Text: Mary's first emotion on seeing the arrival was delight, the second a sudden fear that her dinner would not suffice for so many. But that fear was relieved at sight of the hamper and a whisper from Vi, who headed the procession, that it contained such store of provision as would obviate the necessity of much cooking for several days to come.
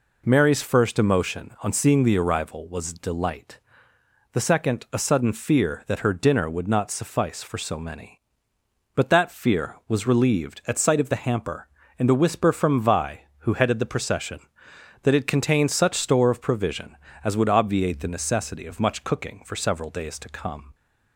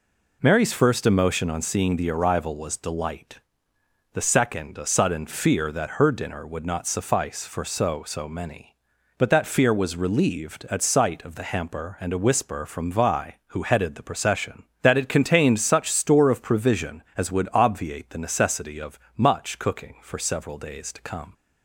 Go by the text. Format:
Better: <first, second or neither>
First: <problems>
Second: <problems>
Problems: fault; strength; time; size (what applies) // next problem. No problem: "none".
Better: first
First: none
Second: says "so" twice; at 8.0 s // pauses between "of" and "much"; slight; at 18.9 s; 0.20 s long